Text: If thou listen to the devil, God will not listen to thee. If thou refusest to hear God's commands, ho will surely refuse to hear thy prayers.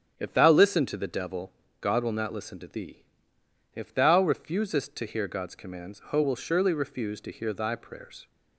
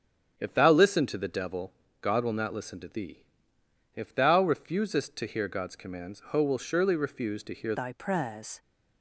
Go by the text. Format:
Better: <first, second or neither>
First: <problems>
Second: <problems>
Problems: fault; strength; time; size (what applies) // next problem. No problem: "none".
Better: first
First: starts louder than the rest; strong; until 1.1 s; 8.5 dB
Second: starts louder than the rest; strong; until 1.3 s; 8.5 dB // changes voice at "thy"; from 7.7 s on; 0.9 s long